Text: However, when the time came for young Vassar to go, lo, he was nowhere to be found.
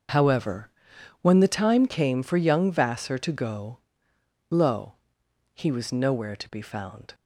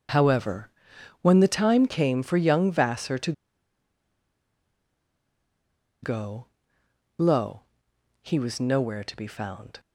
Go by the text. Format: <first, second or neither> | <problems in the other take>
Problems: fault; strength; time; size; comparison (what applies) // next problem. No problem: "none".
first | starts louder than the rest; noticeable; until 1.6 s; 6 dB; noticeable in the first // pauses between "to" and "go"; strong; at 3.3 s; 2.7 s long